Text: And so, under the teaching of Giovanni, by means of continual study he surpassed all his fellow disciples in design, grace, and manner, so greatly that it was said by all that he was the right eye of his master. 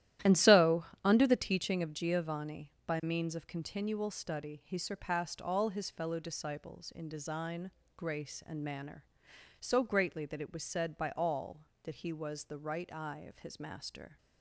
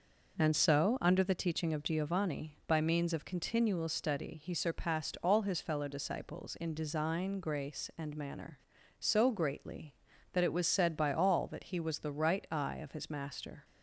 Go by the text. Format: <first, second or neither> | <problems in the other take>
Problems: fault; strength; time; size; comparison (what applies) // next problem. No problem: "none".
second | starts louder than the rest; strong; until 1.8 s; 13 dB